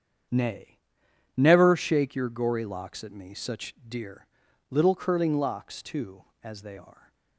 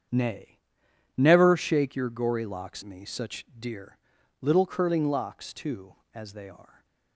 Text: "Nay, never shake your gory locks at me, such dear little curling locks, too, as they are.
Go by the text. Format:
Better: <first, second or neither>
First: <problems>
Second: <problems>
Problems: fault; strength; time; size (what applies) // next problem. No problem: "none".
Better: first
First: starts louder than the rest; strong; until 1.9 s; 8.5 dB // pauses between "dear" and "little"; at 4.2 s; 0.42 s long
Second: starts louder than the rest; strong; until 1.7 s; 8 dB // skips "at"; at 2.8 s // pauses between "dear" and "little"; at 3.9 s; 0.42 s long